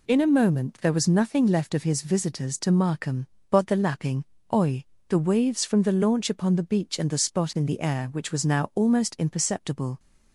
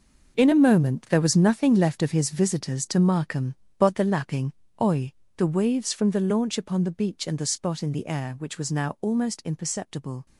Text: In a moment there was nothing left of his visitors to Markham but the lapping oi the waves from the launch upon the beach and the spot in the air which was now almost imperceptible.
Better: first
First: pauses between "lapping" and "oi"; slight; at 4.2 s; 0.30 s long // pauses between "oi" and "the"; slight; at 4.8 s; 0.24 s long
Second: gets quieter; strong; throughout; 12.5 dB // pauses between "lapping" and "oi"; slight; at 4.5 s; 0.30 s long // pauses between "oi" and "the"; slight; at 5.1 s; 0.24 s long

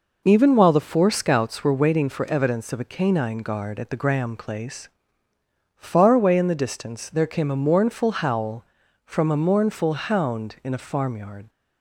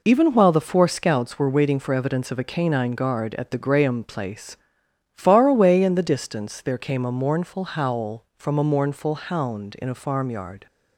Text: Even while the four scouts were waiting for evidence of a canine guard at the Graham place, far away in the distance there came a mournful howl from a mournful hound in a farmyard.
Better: neither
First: none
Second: none

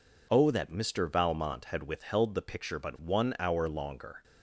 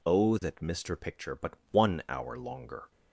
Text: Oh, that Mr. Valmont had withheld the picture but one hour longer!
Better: first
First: none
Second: skips "Valmont had withheld the"; at 0.9 s // pauses between "but" and "one"; slight; at 1.5 s; 0.16 s long

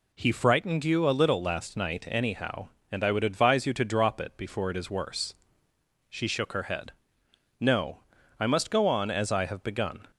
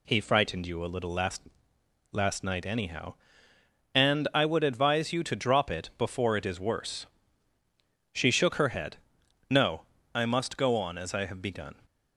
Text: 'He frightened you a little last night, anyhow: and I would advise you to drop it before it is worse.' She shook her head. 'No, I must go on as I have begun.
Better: first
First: none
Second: says "last" twice; at 2.1 s

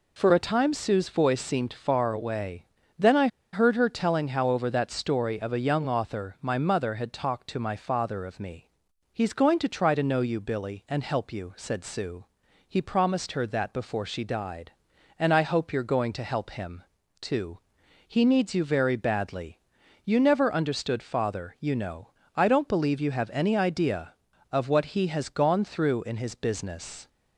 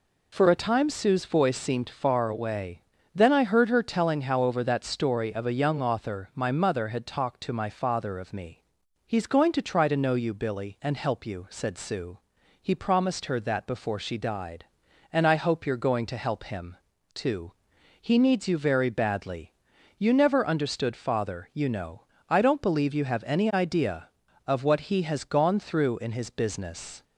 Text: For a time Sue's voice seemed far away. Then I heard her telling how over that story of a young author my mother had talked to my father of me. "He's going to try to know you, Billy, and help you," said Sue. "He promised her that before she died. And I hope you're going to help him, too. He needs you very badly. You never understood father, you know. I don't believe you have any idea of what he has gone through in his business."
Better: second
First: pauses between "I" and "heard"; slight; at 3.2 s; 0.25 s long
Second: none

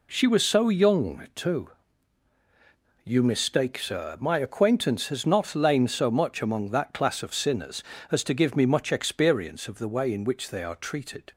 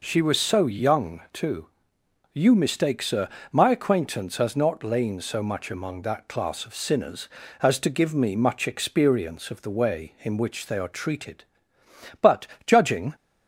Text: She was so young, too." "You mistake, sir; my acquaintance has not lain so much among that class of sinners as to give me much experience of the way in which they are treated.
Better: first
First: none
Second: goes on to say "But judging"; noticeable; from 12.2 s on; 0.94 s long

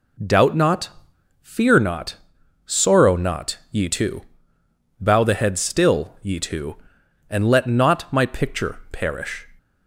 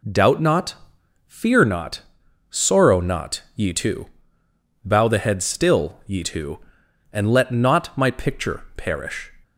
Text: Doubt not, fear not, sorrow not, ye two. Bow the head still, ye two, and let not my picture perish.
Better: neither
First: none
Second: none

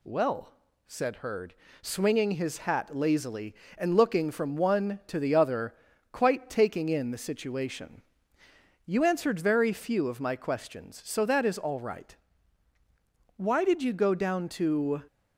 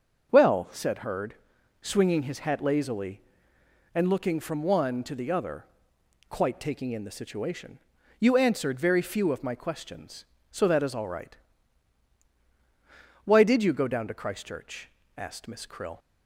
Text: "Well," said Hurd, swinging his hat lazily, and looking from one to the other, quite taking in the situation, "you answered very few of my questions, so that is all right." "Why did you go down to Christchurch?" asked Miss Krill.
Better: second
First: stops before "Christchurch asked Miss Krill"; at 15.0 s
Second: none

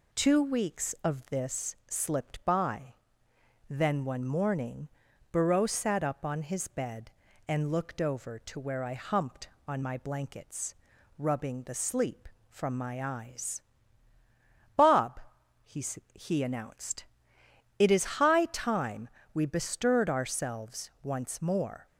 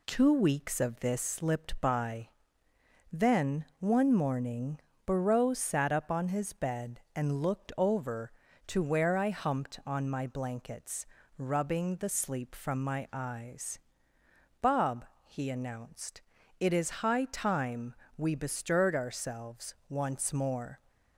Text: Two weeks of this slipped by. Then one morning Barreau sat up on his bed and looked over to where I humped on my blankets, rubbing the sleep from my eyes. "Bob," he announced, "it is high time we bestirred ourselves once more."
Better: second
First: pauses between "morning" and "Barreau"; at 4.8 s; 0.44 s long // says "he" twice; at 16.1 s // pauses between "time" and "we"; slight; at 19.0 s; 0.24 s long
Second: pauses between "morning" and "Barreau"; slight; at 4.7 s; 0.28 s long // pauses between "time" and "we"; slight; at 17.9 s; 0.22 s long

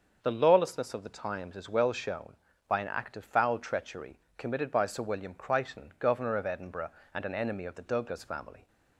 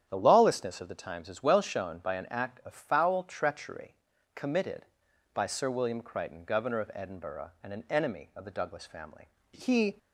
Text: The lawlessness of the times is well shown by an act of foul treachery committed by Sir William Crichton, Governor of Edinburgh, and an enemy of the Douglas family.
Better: first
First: starts louder than the rest; until 1.2 s; 6.5 dB // pauses between "treachery" and "committed"; slight; at 4.1 s; 0.18 s long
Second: starts louder than the rest; strong; until 1.0 s; 9.5 dB // pauses between "treachery" and "committed"; at 3.9 s; 0.42 s long // goes on to say "He"; slight; from 9.5 s on; 0.46 s long

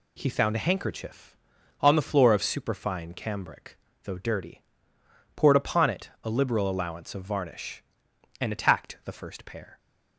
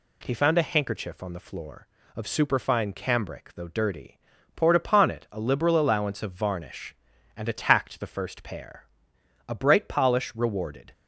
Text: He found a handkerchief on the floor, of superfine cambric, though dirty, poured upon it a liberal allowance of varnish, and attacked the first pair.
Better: first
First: none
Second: goes on to say "A bright polish rewarded"; from 9.4 s on; 1.4 s long

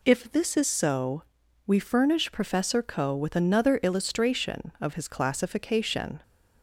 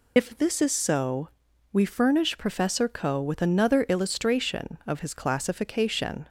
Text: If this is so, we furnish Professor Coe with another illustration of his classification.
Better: first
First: none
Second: loses the start of "If"; at 0.1 s; 65 ms

